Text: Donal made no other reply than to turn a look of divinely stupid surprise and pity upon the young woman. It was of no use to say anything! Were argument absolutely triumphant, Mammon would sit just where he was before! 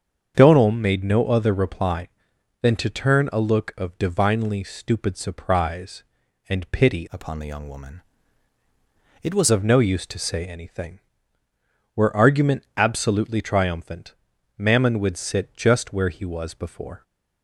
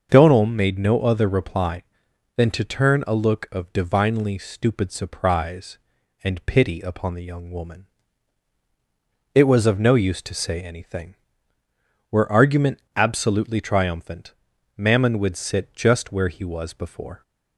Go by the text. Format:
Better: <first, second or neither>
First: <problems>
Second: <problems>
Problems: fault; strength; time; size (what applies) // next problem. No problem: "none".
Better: second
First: starts louder than the rest; strong; until 1.3 s; 7 dB // changes voice from "upon" to "was"; from 7.1 to 9.5 s; 2.4 s long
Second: starts louder than the rest; until 1.1 s; 6.5 dB